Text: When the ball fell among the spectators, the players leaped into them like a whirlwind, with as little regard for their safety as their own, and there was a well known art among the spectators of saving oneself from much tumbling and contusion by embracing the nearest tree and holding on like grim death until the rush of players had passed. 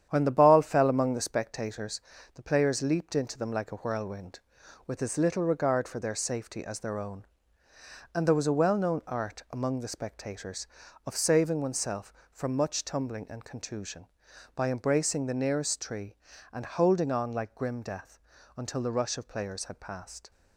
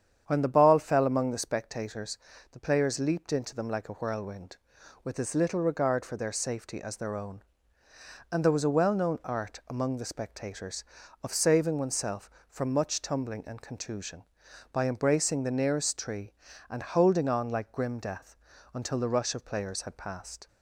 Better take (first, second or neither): second